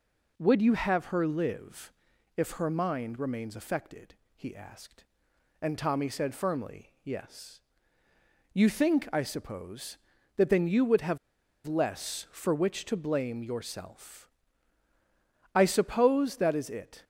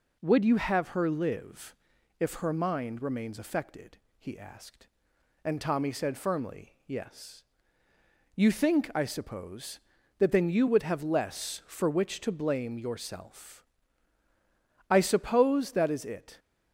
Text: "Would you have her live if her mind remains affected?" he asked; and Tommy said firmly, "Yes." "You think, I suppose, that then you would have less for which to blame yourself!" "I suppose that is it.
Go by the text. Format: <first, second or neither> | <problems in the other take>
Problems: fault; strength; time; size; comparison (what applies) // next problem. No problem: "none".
second | pauses between "live" and "if"; at 1.9 s; 0.42 s long; also in the second // pauses between "have" and "less"; noticeable; at 11.1 s; 0.49 s long